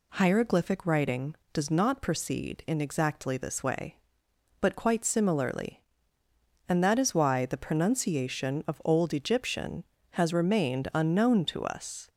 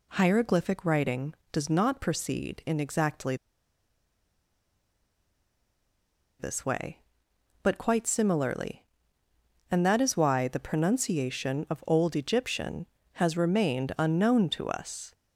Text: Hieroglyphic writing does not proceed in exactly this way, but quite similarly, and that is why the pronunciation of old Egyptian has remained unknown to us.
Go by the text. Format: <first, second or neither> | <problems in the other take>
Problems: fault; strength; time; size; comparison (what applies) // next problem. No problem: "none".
first | pauses between "exactly" and "this"; strong; at 3.3 s; 3.0 s long